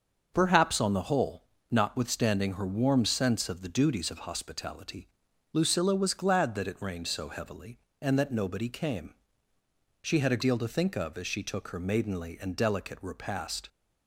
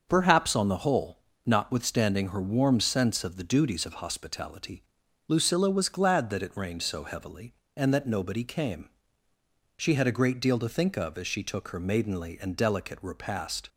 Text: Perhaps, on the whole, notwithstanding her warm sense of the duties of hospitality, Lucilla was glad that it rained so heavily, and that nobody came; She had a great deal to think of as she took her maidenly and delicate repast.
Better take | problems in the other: second | starts louder than the rest; until 1.3 s; 6.5 dB; also in the second // skips "great"; at 10.4 s

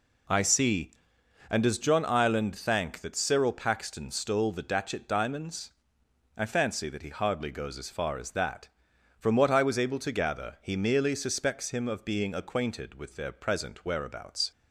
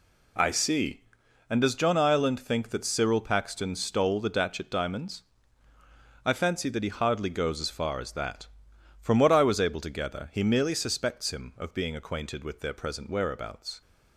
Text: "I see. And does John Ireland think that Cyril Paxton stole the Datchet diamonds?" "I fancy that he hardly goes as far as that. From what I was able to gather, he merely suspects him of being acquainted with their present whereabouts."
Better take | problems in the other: second | says "thank" for "think"; at 2.5 s

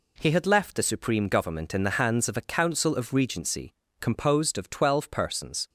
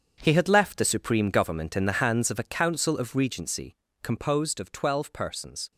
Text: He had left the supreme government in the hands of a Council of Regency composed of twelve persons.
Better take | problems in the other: first | gets quieter; strong; throughout; 10.5 dB // pauses between "Regency" and "composed"; slight; at 3.7 s; 0.28 s long; slight in the first

